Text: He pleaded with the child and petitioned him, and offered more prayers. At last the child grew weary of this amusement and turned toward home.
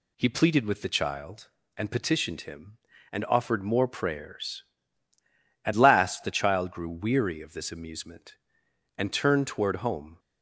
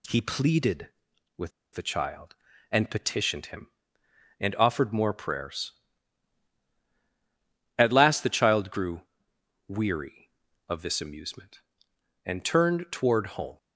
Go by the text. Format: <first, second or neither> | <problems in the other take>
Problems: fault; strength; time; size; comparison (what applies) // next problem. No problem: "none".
first | pauses between "with" and "the"; slight; at 1.5 s; 0.24 s long // pauses between "grew" and "weary"; noticeable; at 9.0 s; 0.68 s long